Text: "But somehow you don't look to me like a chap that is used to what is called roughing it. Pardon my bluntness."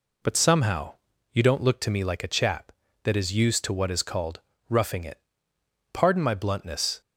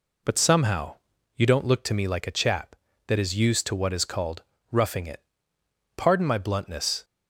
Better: neither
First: pauses between "somehow" and "you"; at 0.9 s; 0.38 s long // pauses between "called" and "roughing"; slight; at 4.3 s; 0.28 s long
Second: pauses between "somehow" and "you"; at 0.9 s; 0.40 s long // pauses between "called" and "roughing"; slight; at 4.4 s; 0.28 s long

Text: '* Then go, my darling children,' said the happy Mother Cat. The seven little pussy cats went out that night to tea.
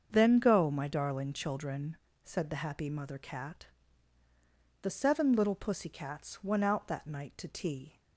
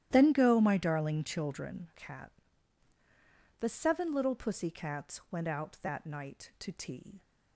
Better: first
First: starts louder than the rest; until 1.1 s; 7 dB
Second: starts louder than the rest; strong; until 1.1 s; 12.5 dB // skips "said the happy Mother"; at 1.9 s

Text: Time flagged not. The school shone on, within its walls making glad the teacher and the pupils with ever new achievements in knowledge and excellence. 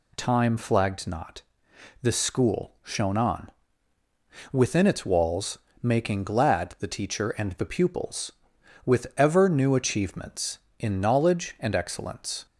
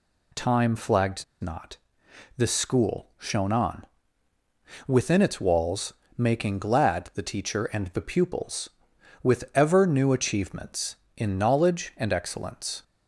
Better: first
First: pauses between "walls" and "making"; slight; at 5.5 s; 0.24 s long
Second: pauses between "flagged" and "not"; slight; at 1.2 s; 0.18 s long // pauses between "walls" and "making"; slight; at 5.9 s; 0.24 s long

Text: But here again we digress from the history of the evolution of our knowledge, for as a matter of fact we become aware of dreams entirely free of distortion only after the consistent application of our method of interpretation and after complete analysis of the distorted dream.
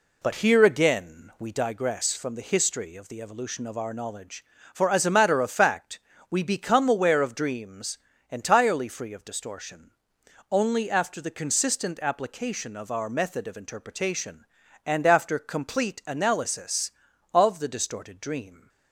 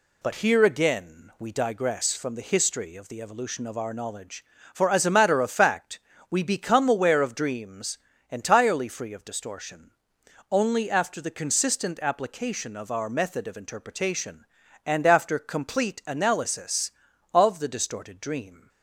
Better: second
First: starts louder than the rest; slight; until 1.6 s; 2 dB // pauses between "fact" and "we"; slight; at 5.9 s; 0.32 s long // pauses between "dreams" and "entirely"; slight; at 7.9 s; 0.32 s long // pauses between "distortion" and "only"; noticeable; at 9.9 s; 0.60 s long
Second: pauses between "fact" and "we"; slight; at 5.9 s; 0.32 s long // pauses between "dreams" and "entirely"; slight; at 7.9 s; 0.32 s long // pauses between "distortion" and "only"; noticeable; at 9.9 s; 0.60 s long

